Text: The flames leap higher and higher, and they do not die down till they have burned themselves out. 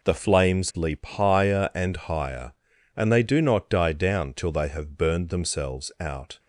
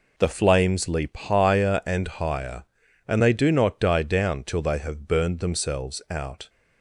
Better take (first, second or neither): neither